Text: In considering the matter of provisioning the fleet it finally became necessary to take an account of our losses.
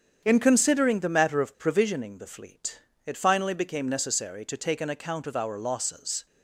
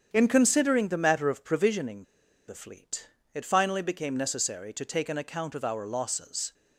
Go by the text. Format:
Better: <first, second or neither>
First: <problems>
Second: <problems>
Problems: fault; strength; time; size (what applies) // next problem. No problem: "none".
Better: first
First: starts louder than the rest; strong; until 1.2 s; 8 dB // pauses between "fleet" and "it"; slight; at 2.7 s; 0.28 s long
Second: starts louder than the rest; strong; until 1.1 s; 8 dB // pauses between "provisioning" and "the"; at 2.0 s; 0.42 s long // pauses between "fleet" and "it"; slight; at 3.0 s; 0.28 s long